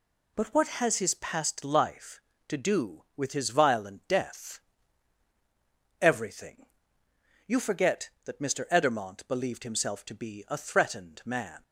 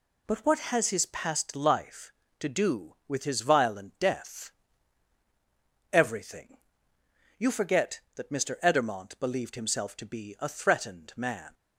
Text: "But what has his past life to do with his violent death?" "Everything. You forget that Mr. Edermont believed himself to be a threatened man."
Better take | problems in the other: neither | none

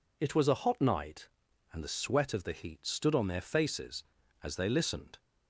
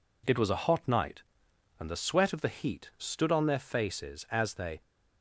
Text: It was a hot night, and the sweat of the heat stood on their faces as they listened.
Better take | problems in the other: first | stops before "listened"; at 4.8 s

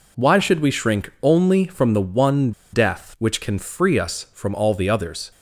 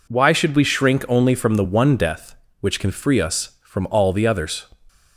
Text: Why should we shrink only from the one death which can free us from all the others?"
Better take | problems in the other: second | pauses between "one" and "death"; slight; at 2.5 s; 0.21 s long

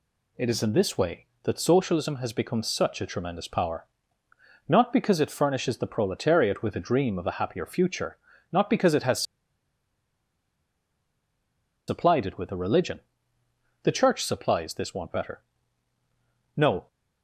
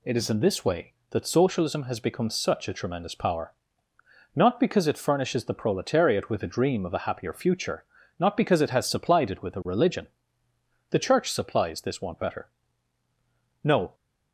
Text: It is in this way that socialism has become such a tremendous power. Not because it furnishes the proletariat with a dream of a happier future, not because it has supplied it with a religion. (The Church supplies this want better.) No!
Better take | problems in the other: second | pauses between "has" and "supplied"; strong; at 9.2 s; 2.6 s long

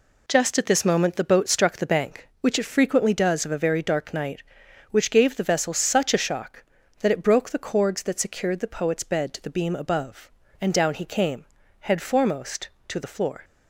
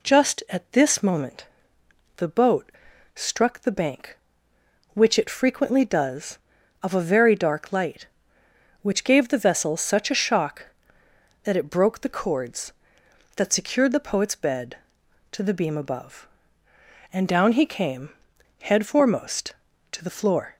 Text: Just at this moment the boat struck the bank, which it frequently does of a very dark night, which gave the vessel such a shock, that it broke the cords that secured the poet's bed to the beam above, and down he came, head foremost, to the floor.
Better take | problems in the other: first | pauses between "moment" and "the"; noticeable; at 1.4 s; 0.70 s long // pauses between "boat" and "struck"; at 2.7 s; 0.44 s long // says "light" for "night"; at 7.7 s

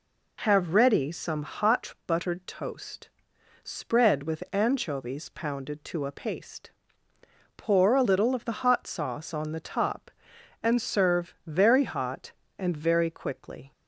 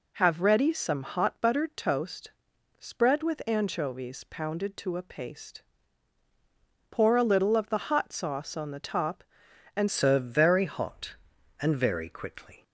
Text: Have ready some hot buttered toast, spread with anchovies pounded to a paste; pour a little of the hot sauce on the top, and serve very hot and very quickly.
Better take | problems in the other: first | changes voice at "serve"; from 9.9 s on; 2.7 s long

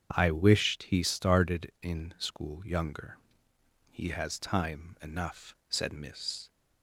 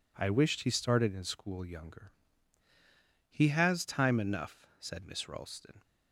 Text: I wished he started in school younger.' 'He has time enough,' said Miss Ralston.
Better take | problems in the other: second | starts louder than the rest; strong; until 1.1 s; 8 dB // stops before "Ralston"; at 6.4 s

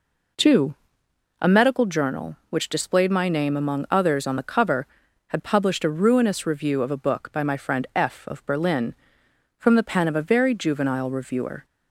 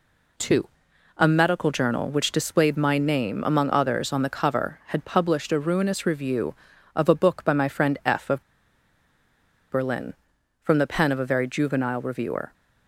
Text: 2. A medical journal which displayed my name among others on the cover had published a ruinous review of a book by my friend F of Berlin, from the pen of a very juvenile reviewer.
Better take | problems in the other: first | pauses between "of" and "Berlin"; strong; at 8.4 s; 1.2 s long

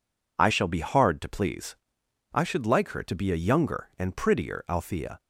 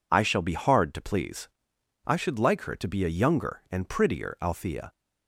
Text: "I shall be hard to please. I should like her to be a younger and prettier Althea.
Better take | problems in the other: neither | none

